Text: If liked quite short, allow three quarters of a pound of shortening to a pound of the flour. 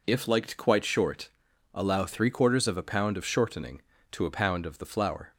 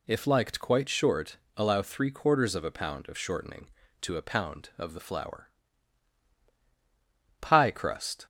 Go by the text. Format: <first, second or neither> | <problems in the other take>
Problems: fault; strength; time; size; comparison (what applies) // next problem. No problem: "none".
first | goes on to say "Pie crust"; noticeable; from 7.3 s on; 0.86 s long